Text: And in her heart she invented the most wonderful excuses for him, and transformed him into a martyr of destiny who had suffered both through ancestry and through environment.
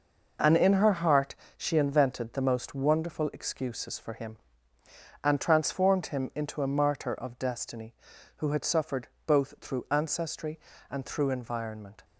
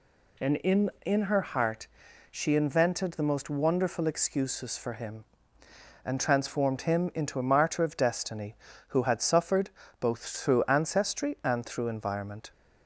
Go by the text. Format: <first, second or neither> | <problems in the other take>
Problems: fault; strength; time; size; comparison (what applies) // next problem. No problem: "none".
first | says "in" twice; at 1.0 s // pauses between "heart" and "she"; at 1.8 s; 0.44 s long; slight in the first // pauses between "suffered" and "both"; slight; at 9.6 s; 0.30 s long; slight in the first